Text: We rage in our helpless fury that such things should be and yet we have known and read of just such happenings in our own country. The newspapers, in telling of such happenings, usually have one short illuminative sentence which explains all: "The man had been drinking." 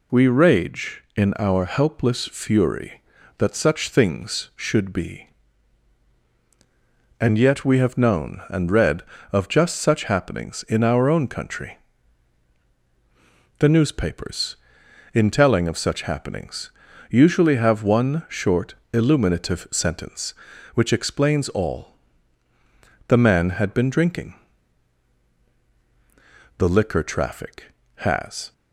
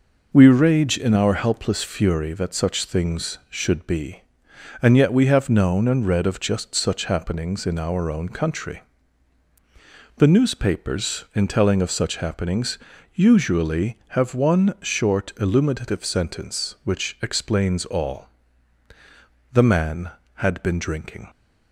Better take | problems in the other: second | pauses between "short" and "illuminative"; slight; at 18.7 s; 0.20 s long // goes on to say "The liquor traffic has"; strong; from 26.5 s on; 1.9 s long

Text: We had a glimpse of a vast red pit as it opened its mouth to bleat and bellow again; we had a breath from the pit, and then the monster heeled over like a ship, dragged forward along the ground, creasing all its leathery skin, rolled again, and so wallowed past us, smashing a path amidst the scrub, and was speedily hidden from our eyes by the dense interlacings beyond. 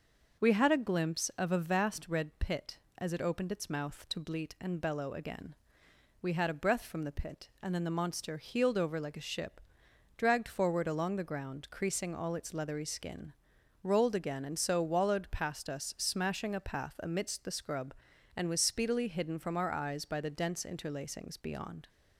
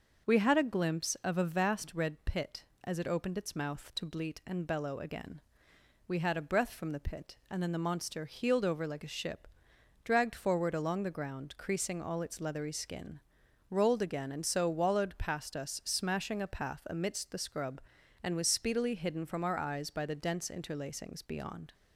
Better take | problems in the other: neither | starts louder than the rest; noticeable; the same in both

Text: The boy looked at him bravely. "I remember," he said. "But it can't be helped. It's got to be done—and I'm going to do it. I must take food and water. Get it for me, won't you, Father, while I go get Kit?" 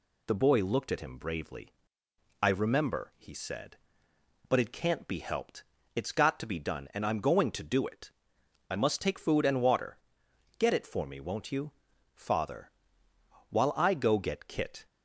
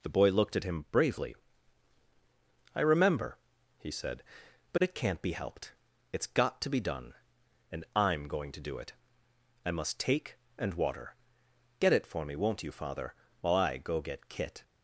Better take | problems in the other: first | skips "food"; at 10.4 s

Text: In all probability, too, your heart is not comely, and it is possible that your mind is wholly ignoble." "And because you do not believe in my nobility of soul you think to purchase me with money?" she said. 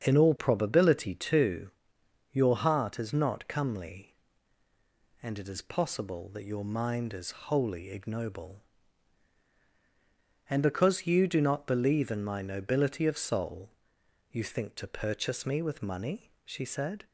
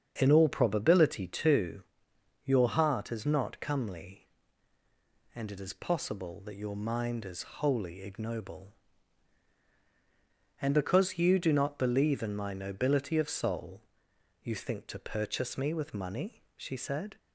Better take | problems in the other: neither | starts louder than the rest; the same in both // pauses between "soul" and "you"; noticeable; the same in both

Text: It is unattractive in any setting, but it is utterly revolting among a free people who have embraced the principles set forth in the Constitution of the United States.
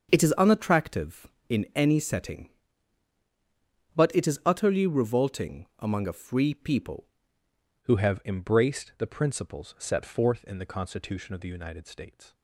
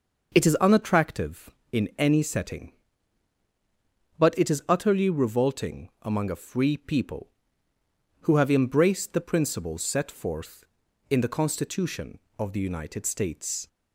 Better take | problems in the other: second | starts louder than the rest; until 1.1 s; 7 dB // changes voice at "who"; from 7.8 s on; 4.5 s long

